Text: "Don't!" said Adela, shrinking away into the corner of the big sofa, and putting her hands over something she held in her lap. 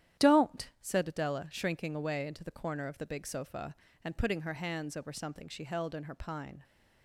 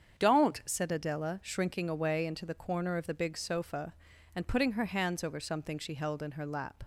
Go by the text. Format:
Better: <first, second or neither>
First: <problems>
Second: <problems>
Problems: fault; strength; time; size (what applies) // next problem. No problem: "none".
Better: second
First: starts louder than the rest; strong; until 1.3 s; 11 dB // says "pine" for "lap"; at 6.1 s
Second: starts louder than the rest; strong; until 1.2 s; 7.5 dB